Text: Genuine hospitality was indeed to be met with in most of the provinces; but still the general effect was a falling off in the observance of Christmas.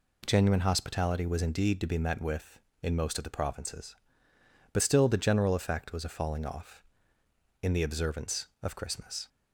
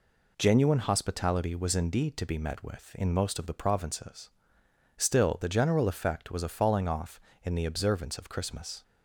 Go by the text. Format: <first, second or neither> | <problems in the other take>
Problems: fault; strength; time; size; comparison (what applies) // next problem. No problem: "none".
first | skips "but"; at 4.6 s